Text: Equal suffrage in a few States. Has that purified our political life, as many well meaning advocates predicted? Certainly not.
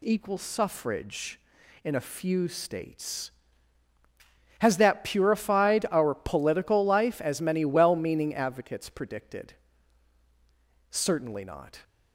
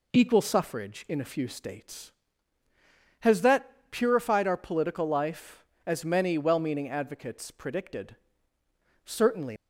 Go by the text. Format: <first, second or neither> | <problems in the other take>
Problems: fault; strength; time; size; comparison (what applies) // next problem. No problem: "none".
first | pauses between "that" and "purified"; slight; at 3.7 s; 0.22 s long // stops before "not"; at 9.5 s